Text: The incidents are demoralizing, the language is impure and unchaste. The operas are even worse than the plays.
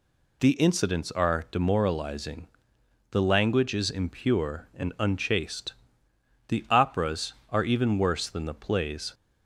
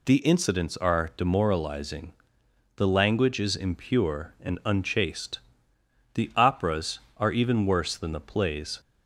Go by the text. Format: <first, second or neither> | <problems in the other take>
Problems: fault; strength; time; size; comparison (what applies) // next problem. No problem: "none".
neither | none